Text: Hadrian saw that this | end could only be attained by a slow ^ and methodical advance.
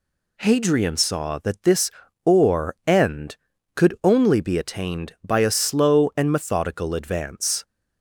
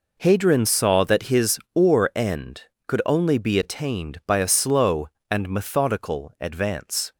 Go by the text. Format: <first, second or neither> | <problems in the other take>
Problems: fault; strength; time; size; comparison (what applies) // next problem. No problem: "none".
first | says "his" for "this"; at 1.2 s